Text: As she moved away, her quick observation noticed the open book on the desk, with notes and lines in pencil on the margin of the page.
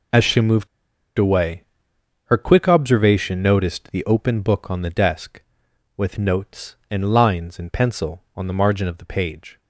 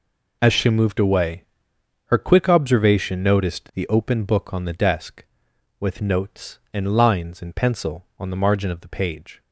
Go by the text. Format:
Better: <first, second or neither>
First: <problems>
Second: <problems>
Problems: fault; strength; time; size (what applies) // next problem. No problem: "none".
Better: second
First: pauses between "moved" and "away"; noticeable; at 0.6 s; 0.51 s long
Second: none